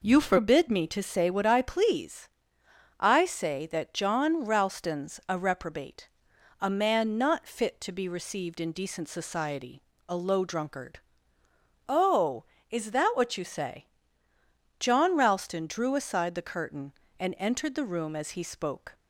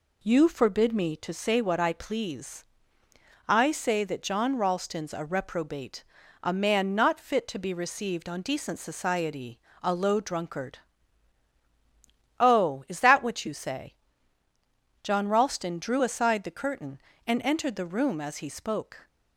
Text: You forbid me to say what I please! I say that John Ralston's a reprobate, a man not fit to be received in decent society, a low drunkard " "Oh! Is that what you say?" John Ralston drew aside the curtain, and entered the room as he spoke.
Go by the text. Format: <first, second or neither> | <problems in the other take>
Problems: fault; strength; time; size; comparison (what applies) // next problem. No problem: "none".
first | says "on" for "in"; at 8.2 s